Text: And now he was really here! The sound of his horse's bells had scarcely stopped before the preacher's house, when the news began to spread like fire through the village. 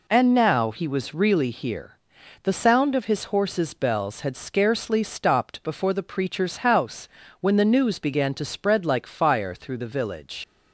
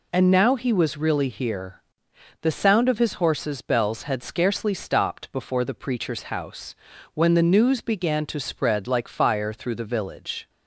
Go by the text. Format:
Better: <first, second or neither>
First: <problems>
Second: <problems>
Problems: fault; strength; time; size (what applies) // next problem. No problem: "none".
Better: second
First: leaves "village" unfinished; at 10.4 s; 90 ms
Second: none